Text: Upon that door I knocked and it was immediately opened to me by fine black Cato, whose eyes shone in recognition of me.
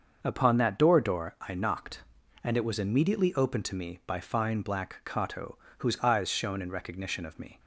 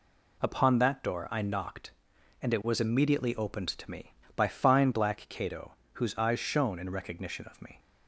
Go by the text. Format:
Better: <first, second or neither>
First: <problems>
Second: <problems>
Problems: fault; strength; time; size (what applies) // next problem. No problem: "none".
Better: second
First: starts louder than the rest; until 1.2 s; 6.5 dB // says "door" twice; at 1.0 s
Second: none